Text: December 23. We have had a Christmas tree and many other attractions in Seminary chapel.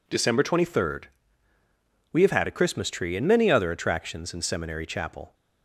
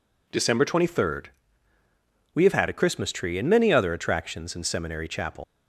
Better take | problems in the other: first | leaves "chapel" unfinished; at 5.4 s; 115 ms

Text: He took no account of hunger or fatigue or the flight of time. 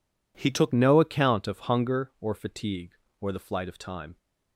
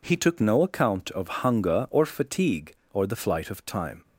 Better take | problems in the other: second | changes voice at "no"; from 0.7 s on; 3.4 s long

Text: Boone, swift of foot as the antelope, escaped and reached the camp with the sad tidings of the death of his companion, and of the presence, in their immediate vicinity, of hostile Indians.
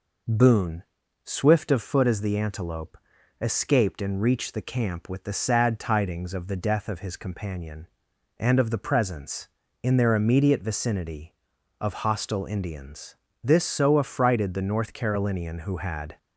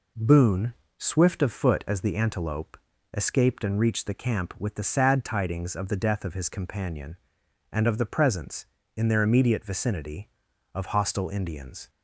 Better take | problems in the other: second | goes on to say "This so affrighted the North Carolinian who had"; strong; from 13.4 s on; 2.7 s long

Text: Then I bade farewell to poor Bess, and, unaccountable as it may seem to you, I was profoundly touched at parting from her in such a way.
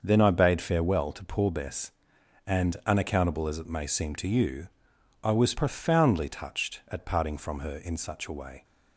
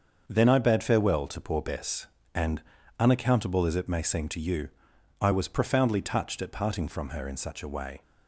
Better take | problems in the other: neither | starts louder than the rest; the same in both

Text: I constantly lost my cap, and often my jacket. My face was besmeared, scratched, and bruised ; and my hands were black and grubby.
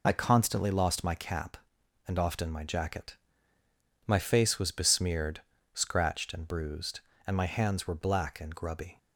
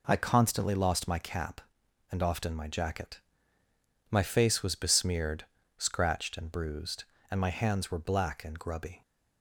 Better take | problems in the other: second | loses the start of "I"; at 0.0 s; 45 ms

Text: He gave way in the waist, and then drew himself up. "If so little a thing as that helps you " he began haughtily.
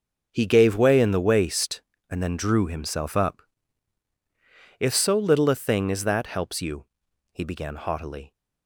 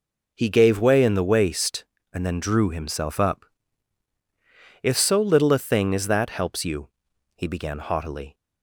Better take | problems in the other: second | gets quieter; strong; throughout; 17 dB

